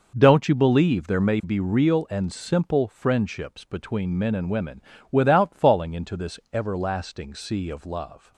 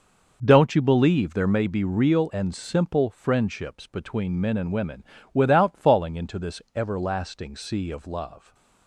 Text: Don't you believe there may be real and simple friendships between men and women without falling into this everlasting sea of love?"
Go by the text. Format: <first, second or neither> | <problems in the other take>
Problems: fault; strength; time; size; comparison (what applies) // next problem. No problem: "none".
neither | pauses between "women" and "without"; slight; the same in both // pauses between "this" and "everlasting"; slight; the same in both